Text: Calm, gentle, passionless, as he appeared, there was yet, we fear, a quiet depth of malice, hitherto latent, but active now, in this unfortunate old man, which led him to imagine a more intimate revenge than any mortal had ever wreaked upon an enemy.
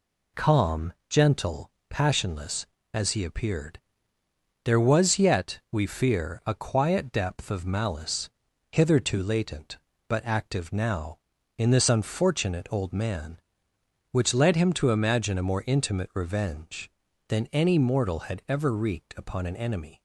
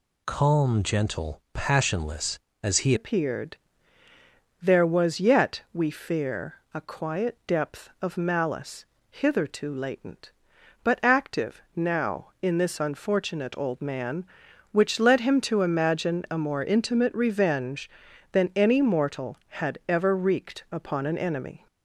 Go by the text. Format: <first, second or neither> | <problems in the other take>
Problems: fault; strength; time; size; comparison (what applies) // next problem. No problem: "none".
first | changes voice at "appeared"; from 2.9 s on; 18.7 s long